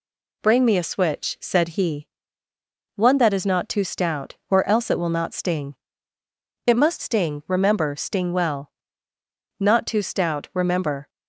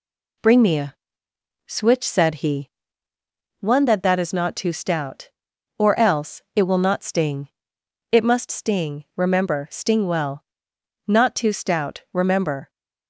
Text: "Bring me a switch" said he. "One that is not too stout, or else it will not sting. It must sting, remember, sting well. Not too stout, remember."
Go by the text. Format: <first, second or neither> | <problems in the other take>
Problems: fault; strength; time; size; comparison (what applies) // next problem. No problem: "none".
first | pauses between "a" and "switch"; noticeable; at 0.9 s; 0.72 s long // says "that" twice; at 4.0 s